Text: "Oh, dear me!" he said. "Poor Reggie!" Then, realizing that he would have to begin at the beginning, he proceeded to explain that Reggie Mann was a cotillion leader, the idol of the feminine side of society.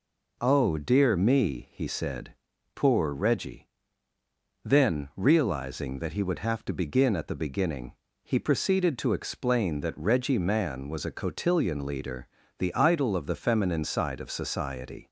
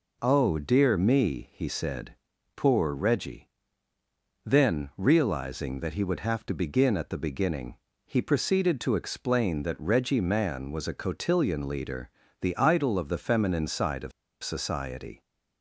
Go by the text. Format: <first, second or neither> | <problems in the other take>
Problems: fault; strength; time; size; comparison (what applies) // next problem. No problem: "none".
first | pauses between "of" and "society"; slight; at 14.1 s; 0.32 s long